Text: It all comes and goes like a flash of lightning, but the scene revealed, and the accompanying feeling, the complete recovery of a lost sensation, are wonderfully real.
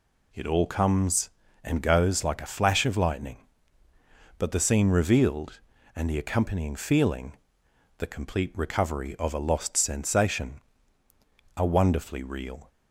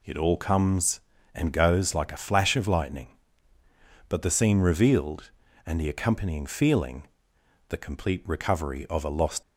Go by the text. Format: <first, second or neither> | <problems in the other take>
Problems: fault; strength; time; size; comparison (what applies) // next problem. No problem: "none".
first | stops before "sensation are wonderfully real"; at 9.4 s